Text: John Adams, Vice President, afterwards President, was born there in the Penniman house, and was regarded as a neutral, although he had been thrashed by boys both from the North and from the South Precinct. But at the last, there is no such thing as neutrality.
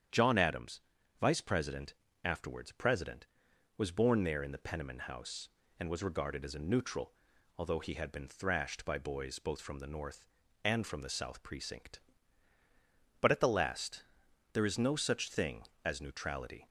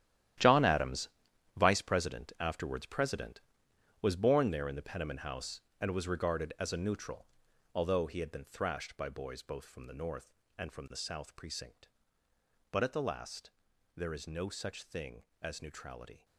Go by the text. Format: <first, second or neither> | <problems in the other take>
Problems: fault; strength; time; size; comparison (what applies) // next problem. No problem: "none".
first | gets quieter; strong; throughout; 13 dB // starts louder than the rest; strong; until 1.8 s; 12 dB; strong in the first